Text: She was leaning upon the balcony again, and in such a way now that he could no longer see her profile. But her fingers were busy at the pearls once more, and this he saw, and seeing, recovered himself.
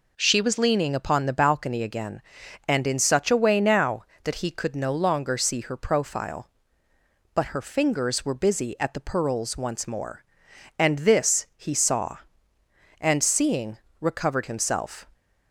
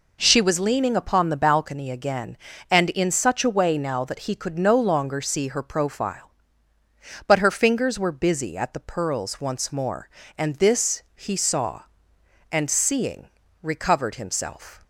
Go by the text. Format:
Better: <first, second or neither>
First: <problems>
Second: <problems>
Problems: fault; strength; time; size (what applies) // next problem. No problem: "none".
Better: neither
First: none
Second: none